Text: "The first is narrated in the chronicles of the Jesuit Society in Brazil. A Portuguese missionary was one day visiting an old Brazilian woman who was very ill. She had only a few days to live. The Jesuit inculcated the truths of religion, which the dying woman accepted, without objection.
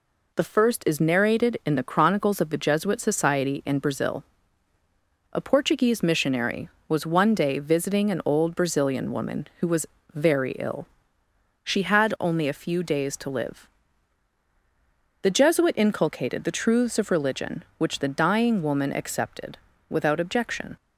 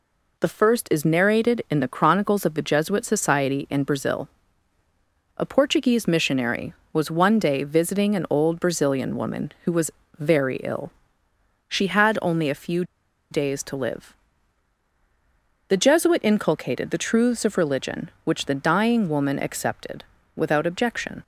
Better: first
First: pauses between "was" and "very"; slight; at 9.8 s; 0.26 s long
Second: pauses between "was" and "very"; slight; at 9.9 s; 0.26 s long // pauses between "few" and "days"; noticeable; at 12.8 s; 0.47 s long

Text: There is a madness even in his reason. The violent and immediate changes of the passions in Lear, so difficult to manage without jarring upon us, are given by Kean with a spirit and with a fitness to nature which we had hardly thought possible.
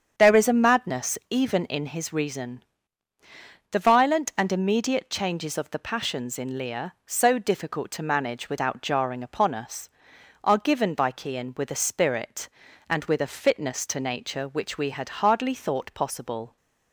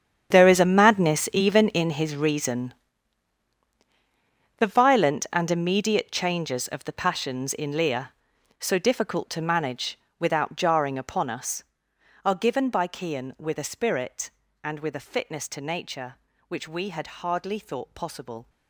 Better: first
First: starts louder than the rest; strong; until 1.1 s; 7.5 dB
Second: gets quieter; strong; throughout; 16 dB // starts louder than the rest; strong; until 1.3 s; 8.5 dB // pauses between "manage" and "without"; slight; at 9.9 s; 0.20 s long

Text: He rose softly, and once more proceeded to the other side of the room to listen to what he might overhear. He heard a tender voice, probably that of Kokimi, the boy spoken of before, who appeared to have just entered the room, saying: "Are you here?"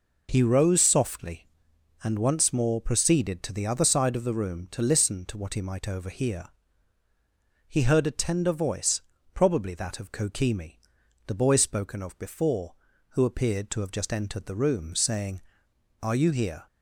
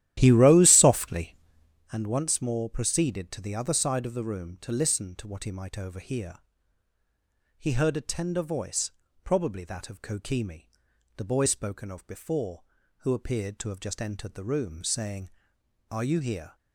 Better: first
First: none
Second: starts louder than the rest; strong; until 1.9 s; 13 dB

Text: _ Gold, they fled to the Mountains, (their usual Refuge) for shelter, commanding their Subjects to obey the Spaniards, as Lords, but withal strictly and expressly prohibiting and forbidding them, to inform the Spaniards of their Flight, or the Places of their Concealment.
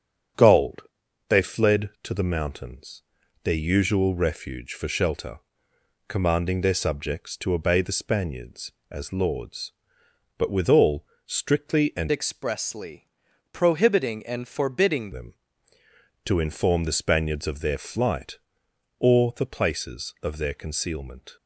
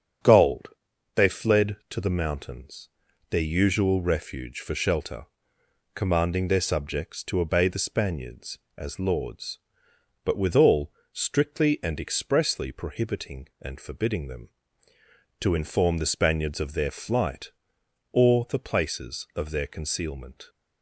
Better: second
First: starts louder than the rest; strong; until 1.8 s; 7.5 dB // pauses between "withal" and "strictly"; slight; at 11.0 s; 0.20 s long // changes voice from "expressly" to "forbidding"; from 12.1 to 15.1 s; 3.0 s long // pauses between "expressly" and "prohibiting"; noticeable; at 13.0 s; 0.46 s long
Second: starts louder than the rest; strong; until 1.7 s; 7.5 dB // pauses between "withal" and "strictly"; slight; at 10.9 s; 0.20 s long

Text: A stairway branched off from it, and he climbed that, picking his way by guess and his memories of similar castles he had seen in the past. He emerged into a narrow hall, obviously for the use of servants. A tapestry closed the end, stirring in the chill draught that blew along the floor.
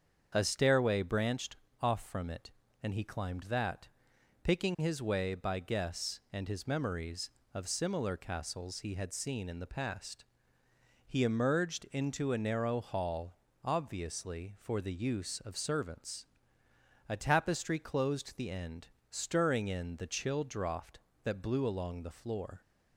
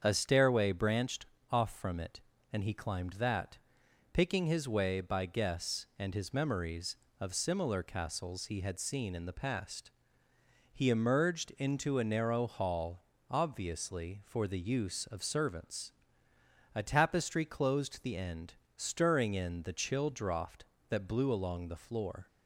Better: neither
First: starts louder than the rest; strong; until 1.3 s; 7 dB // pauses between "branched" and "off"; slight; at 1.5 s; 0.24 s long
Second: starts louder than the rest; strong; until 1.0 s; 7.5 dB // pauses between "branched" and "off"; slight; at 1.2 s; 0.24 s long

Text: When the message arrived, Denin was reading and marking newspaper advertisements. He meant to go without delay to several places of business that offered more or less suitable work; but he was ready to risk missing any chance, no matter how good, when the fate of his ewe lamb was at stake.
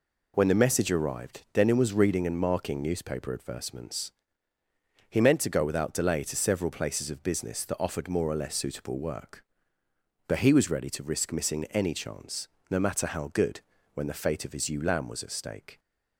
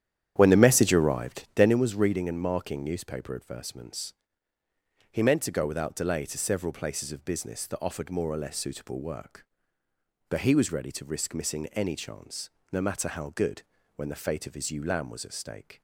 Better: first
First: none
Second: starts louder than the rest; strong; until 1.8 s; 10 dB

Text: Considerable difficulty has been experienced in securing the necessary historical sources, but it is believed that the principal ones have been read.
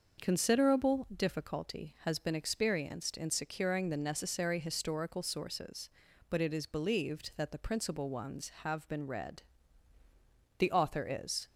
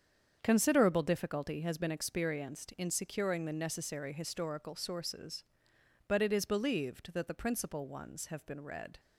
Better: second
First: starts louder than the rest; until 1.2 s; 6 dB // goes on to say "The author is"; noticeable; from 10.5 s on; 0.92 s long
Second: starts louder than the rest; strong; until 1.4 s; 7.5 dB

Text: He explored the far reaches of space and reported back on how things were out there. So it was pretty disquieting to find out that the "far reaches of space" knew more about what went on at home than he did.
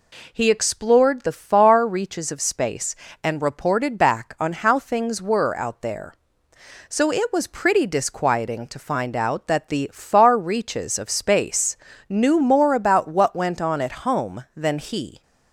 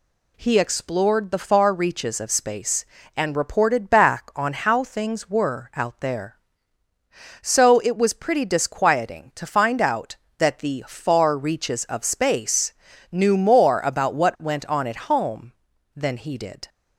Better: second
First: pauses between "space" and "knew"; slight; at 11.7 s; 0.32 s long // stops before "did"; at 15.2 s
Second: pauses between "space" and "knew"; at 12.7 s; 0.38 s long

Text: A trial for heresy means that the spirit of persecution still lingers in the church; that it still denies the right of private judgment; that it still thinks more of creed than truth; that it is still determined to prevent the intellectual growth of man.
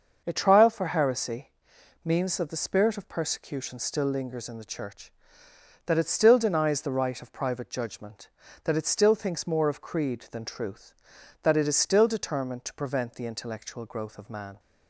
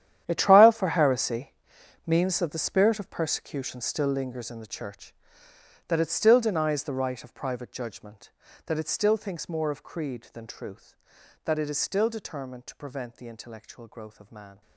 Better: first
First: starts louder than the rest; until 1.2 s; 6.5 dB // pauses between "heresy" and "means"; noticeable; at 1.5 s; 0.54 s long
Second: gets quieter; strong; throughout; 16 dB // starts louder than the rest; strong; until 1.2 s; 10.5 dB // pauses between "heresy" and "means"; noticeable; at 1.5 s; 0.54 s long

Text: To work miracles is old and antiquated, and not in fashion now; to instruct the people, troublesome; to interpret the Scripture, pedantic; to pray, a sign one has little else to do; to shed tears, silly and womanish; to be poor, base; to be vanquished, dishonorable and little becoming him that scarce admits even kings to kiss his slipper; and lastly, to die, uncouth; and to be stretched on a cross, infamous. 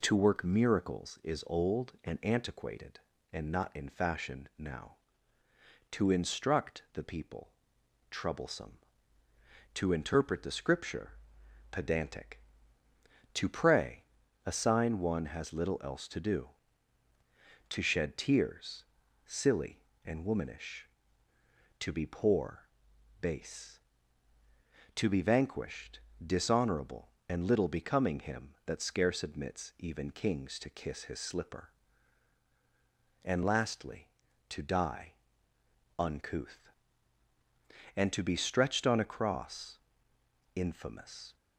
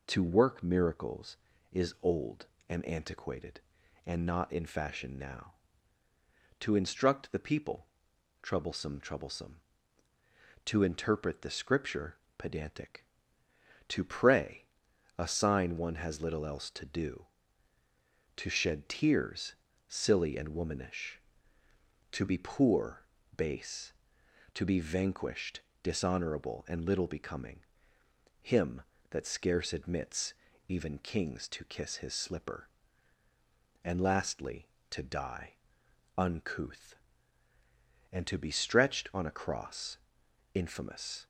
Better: first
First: none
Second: says "troublesome" twice; at 8.9 s // pauses between "becoming" and "him"; noticeable; at 27.5 s; 0.82 s long // pauses between "admits" and "even"; slight; at 30.3 s; 0.34 s long

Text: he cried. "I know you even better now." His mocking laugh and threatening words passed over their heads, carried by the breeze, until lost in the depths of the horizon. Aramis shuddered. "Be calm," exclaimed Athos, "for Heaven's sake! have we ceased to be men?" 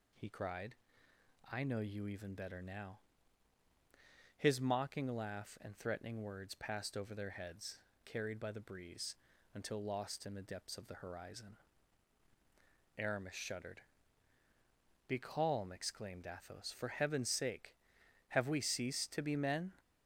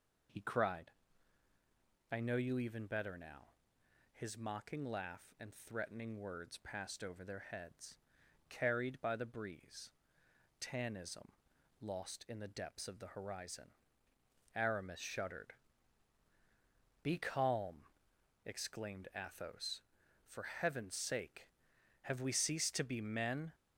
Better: first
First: none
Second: says "tanism" for "until"; at 10.6 s

